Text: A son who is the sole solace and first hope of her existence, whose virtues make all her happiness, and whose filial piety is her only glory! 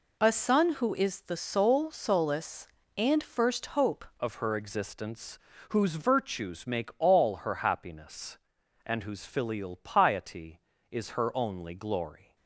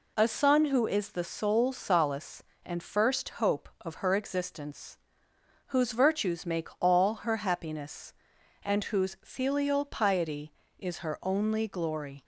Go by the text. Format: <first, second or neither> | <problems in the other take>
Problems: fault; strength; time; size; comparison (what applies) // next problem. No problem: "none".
second | changes voice at "of"; from 4.1 s on; 8.2 s long